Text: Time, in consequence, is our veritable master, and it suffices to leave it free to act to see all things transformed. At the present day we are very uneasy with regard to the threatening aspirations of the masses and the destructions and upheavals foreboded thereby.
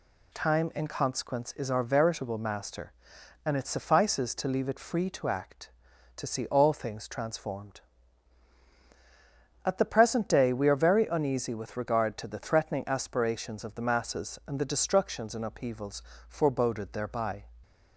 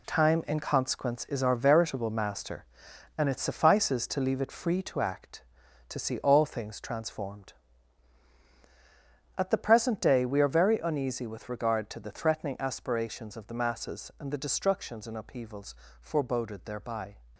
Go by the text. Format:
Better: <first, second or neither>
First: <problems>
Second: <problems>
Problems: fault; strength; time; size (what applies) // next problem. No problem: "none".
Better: first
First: pauses between "upheavals" and "foreboded"; slight; at 16.0 s; 0.26 s long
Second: gets quieter; strong; throughout; 8.5 dB // pauses between "upheavals" and "foreboded"; slight; at 15.7 s; 0.26 s long